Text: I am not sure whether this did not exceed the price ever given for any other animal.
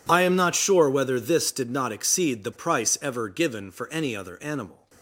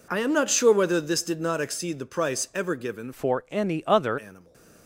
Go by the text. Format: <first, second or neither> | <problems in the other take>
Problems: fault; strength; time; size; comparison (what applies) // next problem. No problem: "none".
first | changes voice from "for" to "other"; from 3.1 to 4.1 s; 1.0 s long // stays silent after the last word; slight; from 4.3 s on; 0.5 s long